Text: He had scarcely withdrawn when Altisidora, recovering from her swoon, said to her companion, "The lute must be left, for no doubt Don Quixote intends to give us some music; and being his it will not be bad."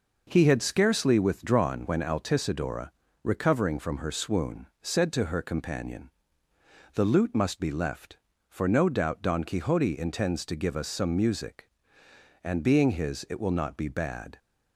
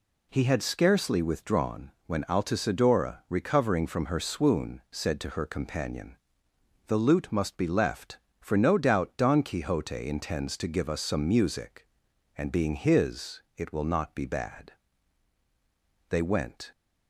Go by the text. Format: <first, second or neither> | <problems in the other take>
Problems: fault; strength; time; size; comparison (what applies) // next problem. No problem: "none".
first | pauses between "withdrawn" and "when"; slight; at 1.9 s; 0.16 s long // goes on to say "They went"; from 16.1 s on; 0.60 s long